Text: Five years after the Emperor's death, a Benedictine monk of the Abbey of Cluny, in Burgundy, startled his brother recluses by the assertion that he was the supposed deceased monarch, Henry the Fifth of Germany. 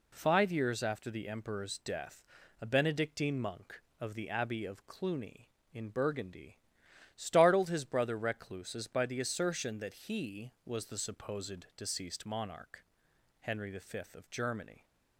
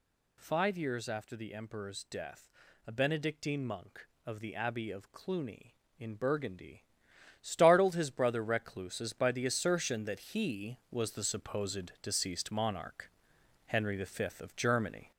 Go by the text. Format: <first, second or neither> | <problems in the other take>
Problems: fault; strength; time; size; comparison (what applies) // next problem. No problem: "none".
first | gets louder; noticeable; throughout; 5 dB